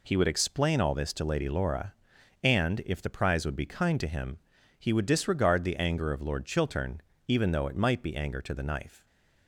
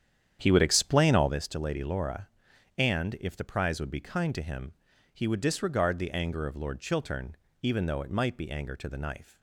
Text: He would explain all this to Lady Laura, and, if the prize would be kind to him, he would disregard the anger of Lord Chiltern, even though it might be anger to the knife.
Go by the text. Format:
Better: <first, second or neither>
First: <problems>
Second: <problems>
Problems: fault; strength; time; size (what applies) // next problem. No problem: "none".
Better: first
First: none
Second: starts louder than the rest; strong; until 1.4 s; 9 dB